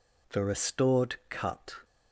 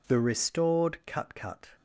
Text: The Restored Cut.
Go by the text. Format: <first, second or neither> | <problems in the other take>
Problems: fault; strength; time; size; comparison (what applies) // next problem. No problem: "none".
first | says "Cut" twice; at 1.3 s